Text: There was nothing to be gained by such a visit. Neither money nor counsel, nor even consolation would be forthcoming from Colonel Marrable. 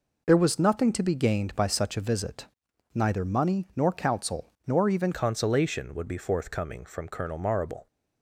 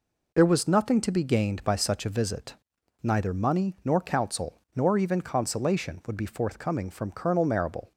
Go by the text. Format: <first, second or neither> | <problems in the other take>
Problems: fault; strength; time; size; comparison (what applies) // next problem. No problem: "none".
second | changes voice at "consolation"; from 5.1 s on; 2.7 s long